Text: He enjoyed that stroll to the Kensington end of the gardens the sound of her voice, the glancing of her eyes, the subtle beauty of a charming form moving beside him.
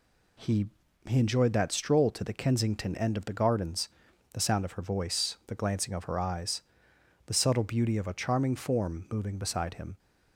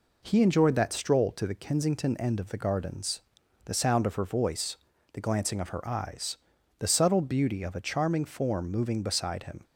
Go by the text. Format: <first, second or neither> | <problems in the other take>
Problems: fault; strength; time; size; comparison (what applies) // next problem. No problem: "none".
second | says "He" twice; at 1.0 s // pauses between "gardens" and "the"; noticeable; at 3.8 s; 0.46 s long; noticeable in the second